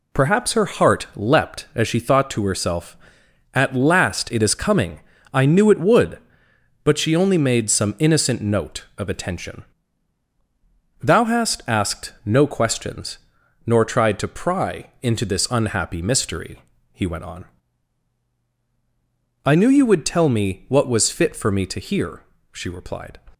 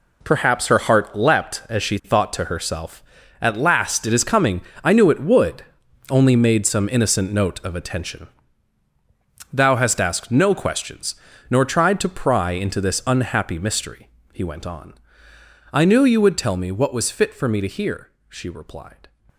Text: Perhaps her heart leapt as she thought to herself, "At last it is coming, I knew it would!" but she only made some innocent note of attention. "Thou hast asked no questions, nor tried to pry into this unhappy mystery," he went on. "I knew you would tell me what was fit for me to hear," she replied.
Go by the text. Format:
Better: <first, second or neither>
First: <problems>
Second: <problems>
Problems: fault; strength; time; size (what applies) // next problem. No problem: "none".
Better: first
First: none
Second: skips "but she"; at 5.8 s